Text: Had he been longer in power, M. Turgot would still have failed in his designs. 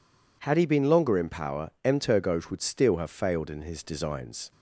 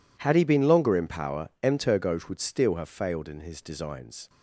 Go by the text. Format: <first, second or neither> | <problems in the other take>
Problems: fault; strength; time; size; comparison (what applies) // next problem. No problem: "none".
first | gets quieter; strong; throughout; 20.5 dB